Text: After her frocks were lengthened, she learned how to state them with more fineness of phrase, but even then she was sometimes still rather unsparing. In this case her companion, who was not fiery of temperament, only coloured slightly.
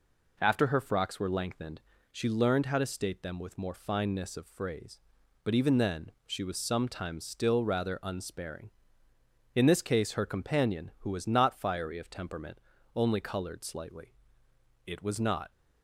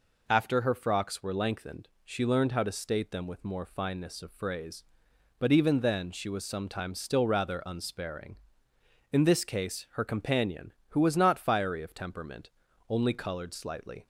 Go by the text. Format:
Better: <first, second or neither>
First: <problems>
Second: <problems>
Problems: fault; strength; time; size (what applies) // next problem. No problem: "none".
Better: second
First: pauses between "then" and "she"; slight; at 6.1 s; 0.16 s long // goes on to say "It was not"; noticeable; from 14.8 s on; 0.64 s long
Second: none